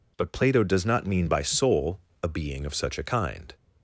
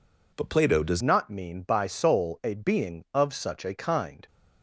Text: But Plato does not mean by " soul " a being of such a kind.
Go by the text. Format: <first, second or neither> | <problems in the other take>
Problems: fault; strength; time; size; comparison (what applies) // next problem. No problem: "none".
first | changes voice at "not"; from 1.0 s on; 3.2 s long